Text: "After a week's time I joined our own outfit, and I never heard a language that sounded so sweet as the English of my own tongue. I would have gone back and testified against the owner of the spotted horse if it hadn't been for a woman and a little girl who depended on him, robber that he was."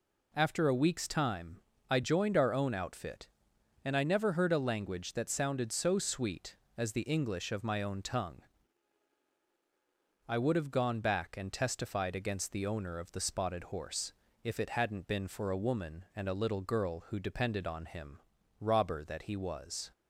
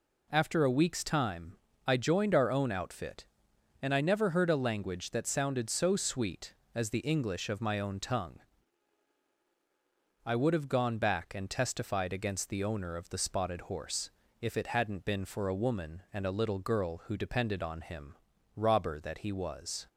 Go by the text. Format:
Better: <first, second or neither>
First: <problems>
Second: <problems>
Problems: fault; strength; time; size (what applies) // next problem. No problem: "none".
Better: neither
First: pauses between "time" and "I"; slight; at 1.5 s; 0.29 s long // pauses between "horse" and "if"; slight; at 14.1 s; 0.30 s long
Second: pauses between "time" and "I"; slight; at 1.5 s; 0.30 s long // pauses between "horse" and "if"; slight; at 14.0 s; 0.30 s long